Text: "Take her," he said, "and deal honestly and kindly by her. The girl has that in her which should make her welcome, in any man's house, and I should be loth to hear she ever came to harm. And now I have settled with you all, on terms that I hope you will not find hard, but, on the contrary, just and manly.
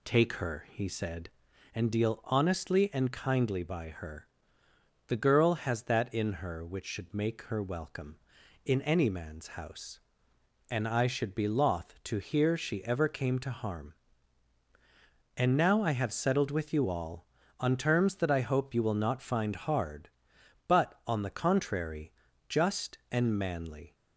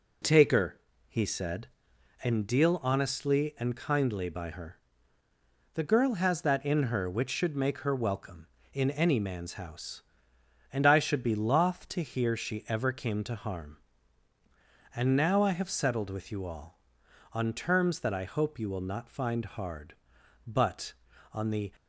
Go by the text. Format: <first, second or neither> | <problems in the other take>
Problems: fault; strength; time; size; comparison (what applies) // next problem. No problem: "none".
first | stops before "contrary just and manly"; at 21.7 s